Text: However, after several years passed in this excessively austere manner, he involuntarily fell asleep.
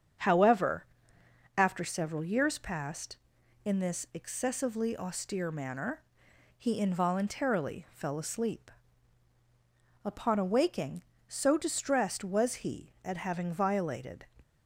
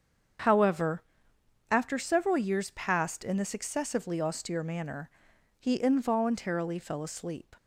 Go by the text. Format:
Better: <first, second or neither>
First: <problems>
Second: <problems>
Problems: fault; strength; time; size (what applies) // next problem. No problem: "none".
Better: second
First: starts louder than the rest; strong; until 1.9 s; 7.5 dB // goes on to say "Upon awaking so distressed was he at having violated"; strong; from 10.0 s on; 4.2 s long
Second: starts louder than the rest; until 2.1 s; 7 dB